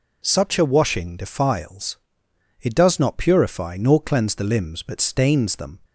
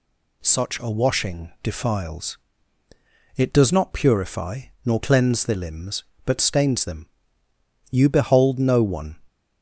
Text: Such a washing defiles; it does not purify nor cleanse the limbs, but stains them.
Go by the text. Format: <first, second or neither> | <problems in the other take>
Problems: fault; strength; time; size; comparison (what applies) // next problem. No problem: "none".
first | pauses between "purify" and "nor"; slight; at 4.6 s; 0.24 s long // goes on to say "You behold no one"; noticeable; from 7.8 s on; 1.2 s long